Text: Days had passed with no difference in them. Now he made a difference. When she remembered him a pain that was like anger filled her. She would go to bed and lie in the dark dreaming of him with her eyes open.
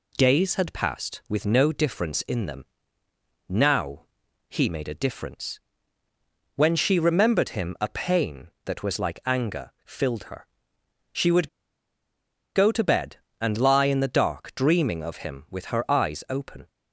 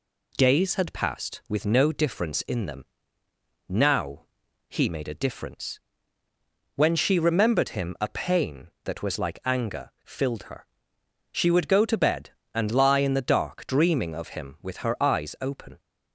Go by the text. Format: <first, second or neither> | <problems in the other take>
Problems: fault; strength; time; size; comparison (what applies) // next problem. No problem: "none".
second | pauses between "Now" and "he"; noticeable; at 4.0 s; 0.46 s long; noticeable in the second // pauses between "would" and "go"; at 11.4 s; 1.0 s long